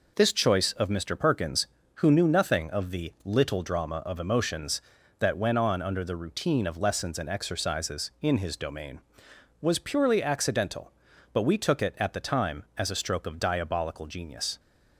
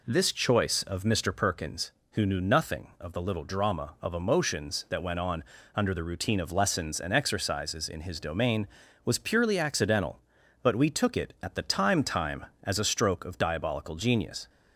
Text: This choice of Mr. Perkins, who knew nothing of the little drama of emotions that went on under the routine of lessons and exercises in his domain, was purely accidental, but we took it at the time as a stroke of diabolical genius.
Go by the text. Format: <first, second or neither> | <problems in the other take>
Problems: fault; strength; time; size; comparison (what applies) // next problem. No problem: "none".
first | pauses between "on" and "under"; slight; at 5.4 s; 0.32 s long // says "time" twice; at 12.0 s